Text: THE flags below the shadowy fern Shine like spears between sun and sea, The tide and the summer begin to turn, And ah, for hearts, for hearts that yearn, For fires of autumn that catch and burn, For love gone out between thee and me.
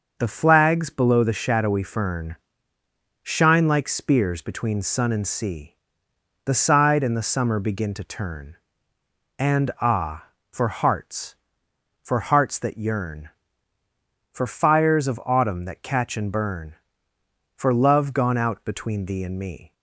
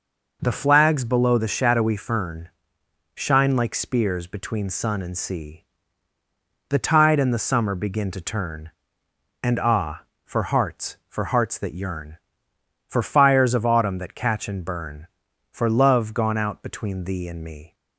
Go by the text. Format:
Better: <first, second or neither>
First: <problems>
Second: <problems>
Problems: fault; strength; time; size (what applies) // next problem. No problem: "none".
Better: second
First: pauses between "fern" and "Shine"; noticeable; at 2.3 s; 0.84 s long // says "side" for "tide"; at 6.5 s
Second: pauses between "fern" and "Shine"; noticeable; at 2.4 s; 0.64 s long